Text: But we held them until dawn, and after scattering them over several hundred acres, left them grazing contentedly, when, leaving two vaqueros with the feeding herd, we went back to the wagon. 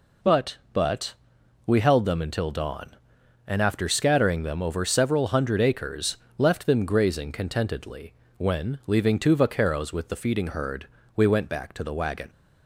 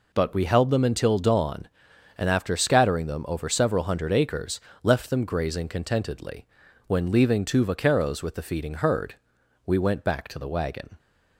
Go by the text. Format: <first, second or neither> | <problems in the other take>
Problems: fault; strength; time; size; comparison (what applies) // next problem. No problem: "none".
second | says "But" twice; at 0.7 s